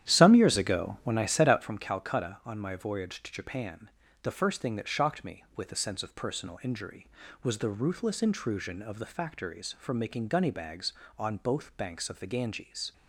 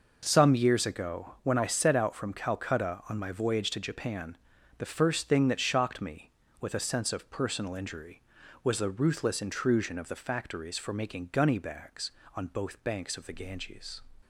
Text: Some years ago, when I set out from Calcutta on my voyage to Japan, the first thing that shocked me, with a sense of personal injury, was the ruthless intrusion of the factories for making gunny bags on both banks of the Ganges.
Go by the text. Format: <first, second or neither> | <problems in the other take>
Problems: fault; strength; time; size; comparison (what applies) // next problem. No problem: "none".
second | starts louder than the rest; strong; until 1.8 s; 11 dB